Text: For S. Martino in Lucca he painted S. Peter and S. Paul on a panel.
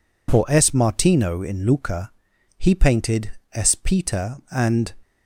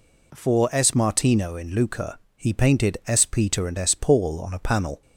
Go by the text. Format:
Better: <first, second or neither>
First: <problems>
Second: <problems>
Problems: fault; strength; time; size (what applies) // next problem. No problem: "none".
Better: second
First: pauses between "Lucca" and "he"; at 2.1 s; 0.44 s long // pauses between "painted" and "S"; slight; at 3.3 s; 0.20 s long // stops before "S Paul on a panel"; at 5.0 s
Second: pauses between "Lucca" and "he"; slight; at 2.1 s; 0.16 s long